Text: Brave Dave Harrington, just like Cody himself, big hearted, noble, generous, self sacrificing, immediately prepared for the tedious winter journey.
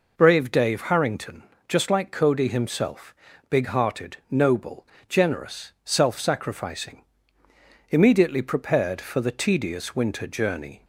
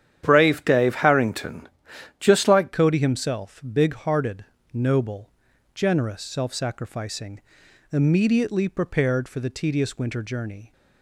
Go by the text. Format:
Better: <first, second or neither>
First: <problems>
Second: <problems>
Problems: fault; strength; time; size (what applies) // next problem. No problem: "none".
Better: first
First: none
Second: starts louder than the rest; strong; until 1.3 s; 10 dB // changes voice at "Cody"; from 2.7 s on; 8.0 s long